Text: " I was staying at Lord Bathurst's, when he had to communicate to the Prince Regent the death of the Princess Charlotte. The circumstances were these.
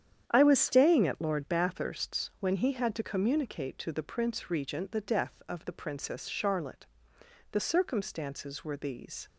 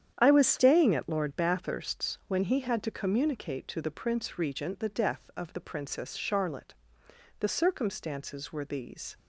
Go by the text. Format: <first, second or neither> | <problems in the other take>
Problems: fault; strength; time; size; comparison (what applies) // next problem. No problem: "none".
neither | starts louder than the rest; strong; the same in both